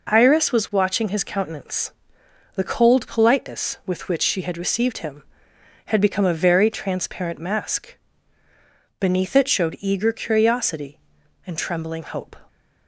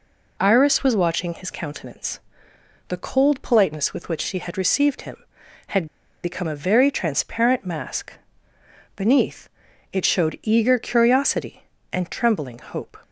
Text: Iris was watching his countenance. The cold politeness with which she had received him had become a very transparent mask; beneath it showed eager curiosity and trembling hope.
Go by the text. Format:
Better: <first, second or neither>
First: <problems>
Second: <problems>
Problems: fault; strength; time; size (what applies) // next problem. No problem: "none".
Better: first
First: none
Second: pauses between "had" and "become"; at 5.8 s; 0.36 s long // pauses between "beneath" and "it"; at 9.4 s; 0.44 s long